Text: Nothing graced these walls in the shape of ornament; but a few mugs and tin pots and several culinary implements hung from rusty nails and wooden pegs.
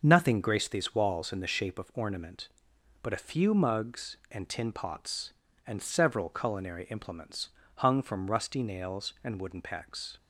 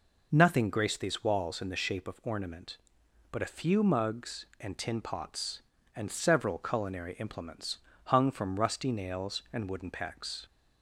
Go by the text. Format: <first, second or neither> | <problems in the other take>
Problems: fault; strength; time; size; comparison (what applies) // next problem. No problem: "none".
second | gets quieter; noticeable; throughout; 5.5 dB // pauses between "implements" and "hung"; slight; at 7.4 s; 0.28 s long; slight in the second